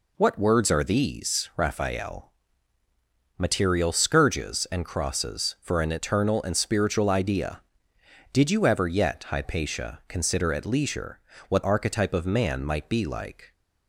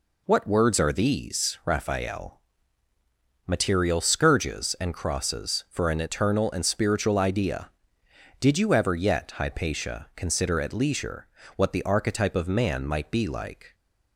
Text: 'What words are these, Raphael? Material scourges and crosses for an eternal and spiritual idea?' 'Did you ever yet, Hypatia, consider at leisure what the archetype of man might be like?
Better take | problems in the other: second | pauses between "leisure" and "what"; slight; at 11.1 s; 0.30 s long; slight in the second // skips "the"; at 11.6 s

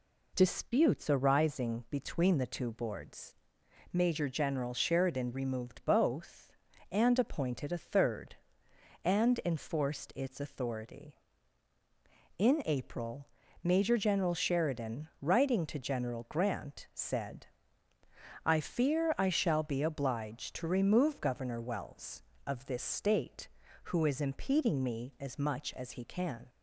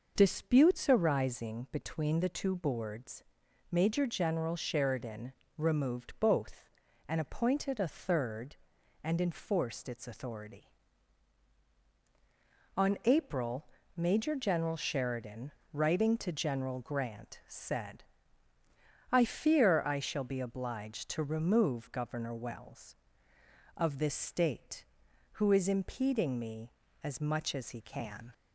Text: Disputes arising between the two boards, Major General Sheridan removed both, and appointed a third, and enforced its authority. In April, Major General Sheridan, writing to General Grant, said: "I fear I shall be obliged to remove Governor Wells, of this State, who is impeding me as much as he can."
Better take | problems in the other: first | pauses between "Sheridan" and "removed"; slight; at 5.3 s; 0.26 s long // says "On" for "In"; at 12.7 s

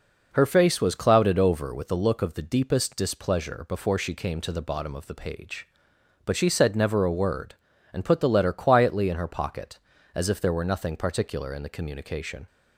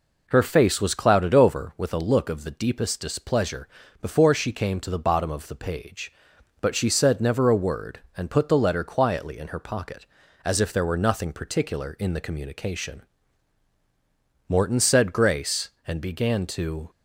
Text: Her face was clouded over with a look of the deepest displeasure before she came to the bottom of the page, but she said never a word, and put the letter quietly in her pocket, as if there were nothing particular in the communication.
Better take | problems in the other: first | pauses between "displeasure" and "before"; slight; at 3.6 s; 0.36 s long // goes on to say "Morton said grace and began to"; strong; from 14.4 s on; 2.4 s long

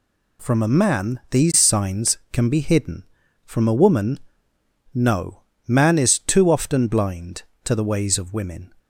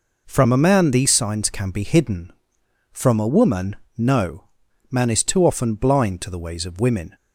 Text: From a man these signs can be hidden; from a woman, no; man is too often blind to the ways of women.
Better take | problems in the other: neither | none

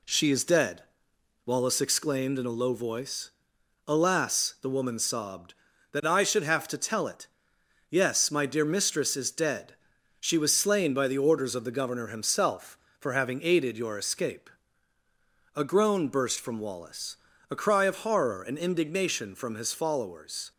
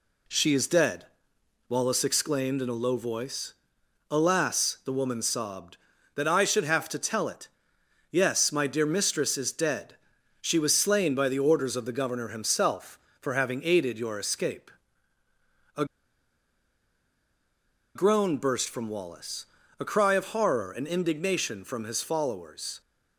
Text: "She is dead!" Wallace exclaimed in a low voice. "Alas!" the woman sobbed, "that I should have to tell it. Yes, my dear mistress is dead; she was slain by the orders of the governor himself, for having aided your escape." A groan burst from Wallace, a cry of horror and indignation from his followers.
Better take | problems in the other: first | pauses between "A" and "groan"; strong; at 15.8 s; 2.1 s long

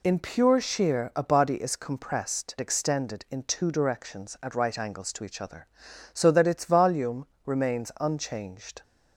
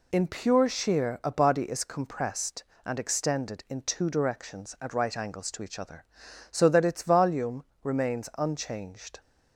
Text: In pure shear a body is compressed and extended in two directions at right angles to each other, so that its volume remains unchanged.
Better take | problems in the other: second | skips "and"; at 2.5 s // pauses between "volume" and "remains"; slight; at 7.2 s; 0.18 s long; slight in the second

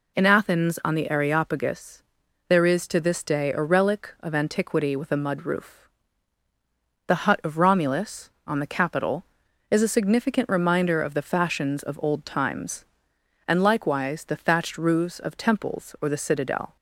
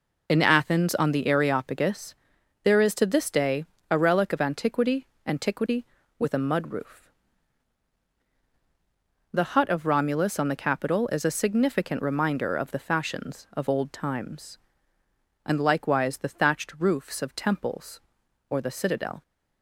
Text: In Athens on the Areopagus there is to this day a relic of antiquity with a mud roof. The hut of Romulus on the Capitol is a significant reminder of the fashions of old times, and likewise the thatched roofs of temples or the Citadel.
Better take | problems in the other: first | pauses between "Areopagus" and "there"; noticeable; at 2.1 s; 0.48 s long; also in the first // pauses between "day" and "a"; slight; at 3.6 s; 0.28 s long // says "antiquity" twice; at 5.2 s

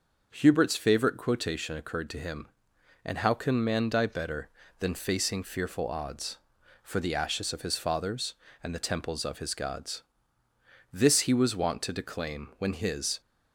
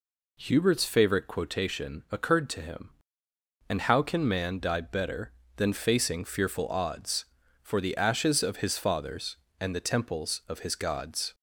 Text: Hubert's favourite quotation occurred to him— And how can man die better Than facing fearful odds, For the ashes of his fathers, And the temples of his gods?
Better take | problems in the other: second | goes on to say "This he was wont to declaim when his"; strong; from 10.9 s on; 2.2 s long

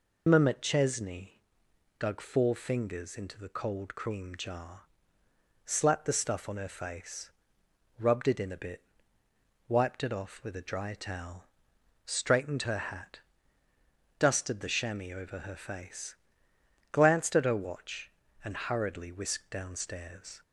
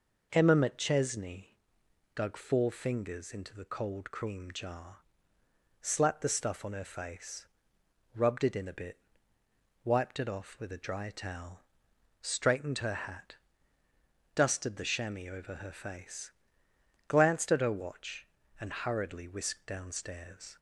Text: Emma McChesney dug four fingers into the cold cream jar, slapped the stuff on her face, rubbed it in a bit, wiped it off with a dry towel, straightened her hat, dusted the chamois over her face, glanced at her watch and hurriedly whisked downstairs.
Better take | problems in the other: second | loses the start of "Emma"; at 0.2 s; 105 ms // pauses between "McChesney" and "dug"; noticeable; at 1.2 s; 0.68 s long; noticeable in the second

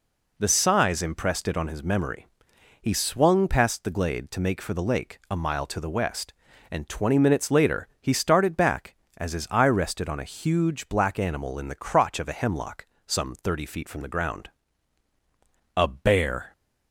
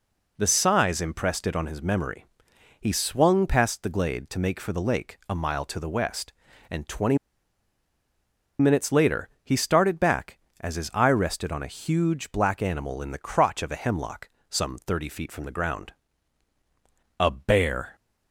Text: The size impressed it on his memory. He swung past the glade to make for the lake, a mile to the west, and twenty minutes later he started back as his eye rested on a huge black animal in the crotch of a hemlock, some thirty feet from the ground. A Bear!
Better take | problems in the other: first | pauses between "twenty" and "minutes"; strong; at 7.1 s; 1.4 s long // pauses between "later" and "he"; slight; at 9.2 s; 0.16 s long

